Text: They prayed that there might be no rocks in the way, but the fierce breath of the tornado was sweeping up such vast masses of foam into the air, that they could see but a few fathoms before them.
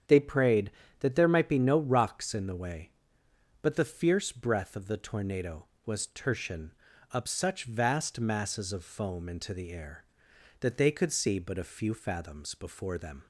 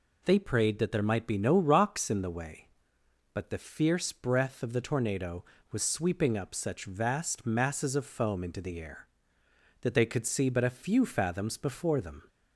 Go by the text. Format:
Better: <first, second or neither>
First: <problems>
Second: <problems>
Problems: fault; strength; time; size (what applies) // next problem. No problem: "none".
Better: second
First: starts louder than the rest; strong; until 1.3 s; 8.5 dB // says "tertian" for "sweeping"; at 6.0 s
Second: none